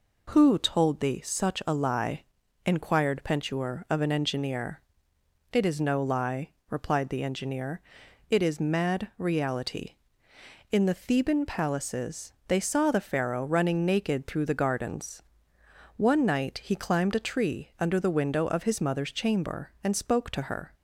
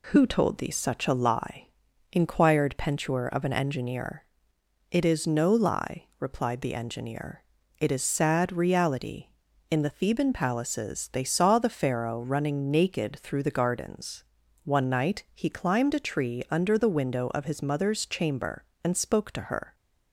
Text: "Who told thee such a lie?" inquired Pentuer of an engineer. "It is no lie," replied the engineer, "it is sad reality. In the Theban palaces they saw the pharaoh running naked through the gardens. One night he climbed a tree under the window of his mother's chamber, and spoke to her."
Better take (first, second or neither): second